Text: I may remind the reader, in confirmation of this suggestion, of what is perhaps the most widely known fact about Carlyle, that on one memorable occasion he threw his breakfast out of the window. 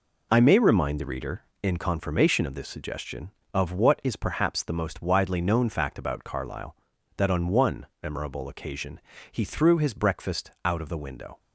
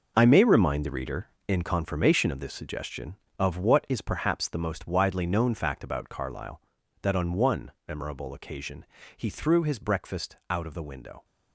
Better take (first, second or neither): first